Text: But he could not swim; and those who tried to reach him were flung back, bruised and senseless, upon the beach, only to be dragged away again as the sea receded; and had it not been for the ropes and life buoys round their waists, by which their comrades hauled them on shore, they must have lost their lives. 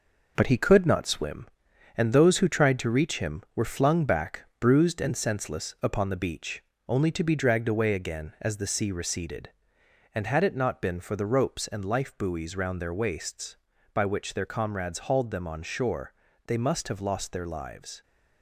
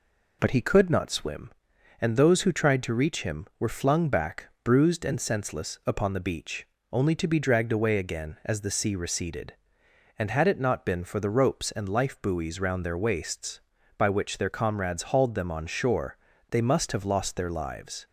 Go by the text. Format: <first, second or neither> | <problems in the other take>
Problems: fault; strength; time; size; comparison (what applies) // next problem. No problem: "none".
second | gets quieter; noticeable; throughout; 6 dB